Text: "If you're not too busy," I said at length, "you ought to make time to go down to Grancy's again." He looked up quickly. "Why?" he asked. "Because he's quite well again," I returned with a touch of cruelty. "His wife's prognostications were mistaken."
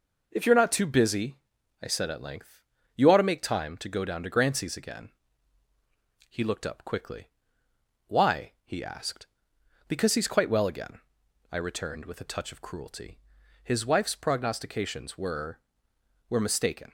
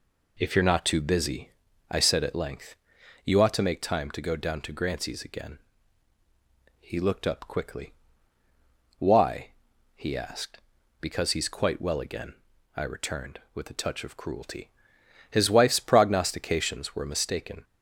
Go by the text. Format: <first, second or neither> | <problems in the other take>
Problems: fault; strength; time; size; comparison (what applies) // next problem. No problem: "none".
second | says "were" twice; at 16.2 s